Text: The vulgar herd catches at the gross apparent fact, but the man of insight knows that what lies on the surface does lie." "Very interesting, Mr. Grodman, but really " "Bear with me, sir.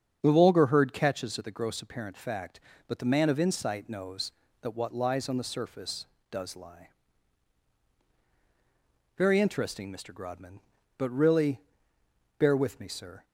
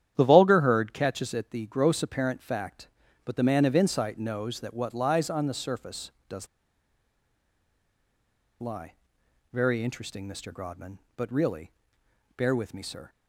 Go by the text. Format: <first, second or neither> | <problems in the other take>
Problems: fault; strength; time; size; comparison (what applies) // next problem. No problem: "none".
first | starts louder than the rest; strong; until 1.1 s; 10.5 dB; strong in the first // pauses between "does" and "lie"; strong; at 6.4 s; 2.1 s long